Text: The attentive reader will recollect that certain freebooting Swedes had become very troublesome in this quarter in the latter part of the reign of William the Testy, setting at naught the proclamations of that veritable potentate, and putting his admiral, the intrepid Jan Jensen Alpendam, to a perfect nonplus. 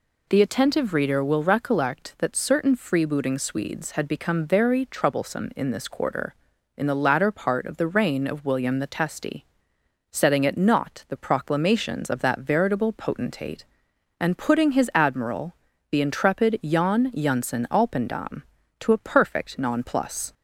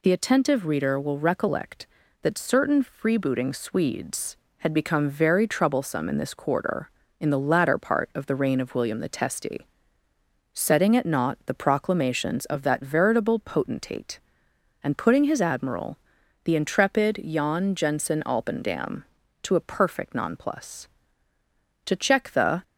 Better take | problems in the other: first | goes on to say "To check the"; noticeable; from 21.8 s on; 0.76 s long

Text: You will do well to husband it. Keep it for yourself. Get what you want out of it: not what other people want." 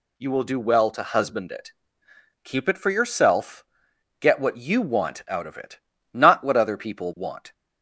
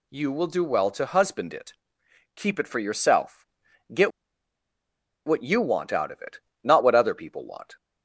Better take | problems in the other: first | pauses between "Get" and "what"; at 4.1 s; 1.1 s long

